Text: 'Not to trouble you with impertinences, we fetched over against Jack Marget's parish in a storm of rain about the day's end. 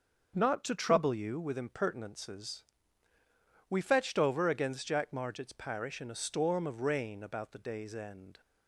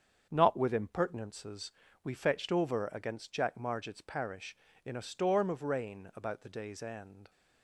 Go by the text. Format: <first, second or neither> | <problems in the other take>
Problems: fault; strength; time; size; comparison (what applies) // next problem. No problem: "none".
first | starts louder than the rest; strong; until 1.3 s; 7.5 dB; also in the first // skips "to trouble you"; at 0.5 s